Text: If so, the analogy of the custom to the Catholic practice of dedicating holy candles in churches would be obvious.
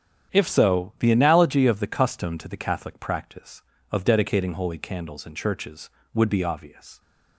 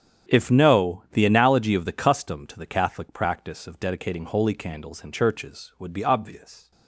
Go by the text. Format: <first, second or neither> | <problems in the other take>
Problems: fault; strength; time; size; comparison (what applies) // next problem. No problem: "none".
first | starts louder than the rest; strong; until 1.3 s; 8.5 dB; strong in the first // says "no" for "so"; at 0.5 s